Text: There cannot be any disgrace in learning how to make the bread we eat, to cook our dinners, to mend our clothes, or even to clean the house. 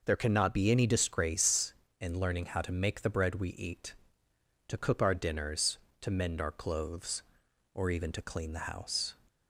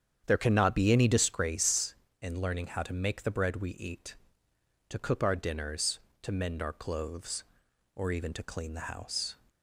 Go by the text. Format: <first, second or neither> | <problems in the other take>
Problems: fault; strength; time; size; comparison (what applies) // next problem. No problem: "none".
first | starts louder than the rest; strong; until 1.4 s; 8.5 dB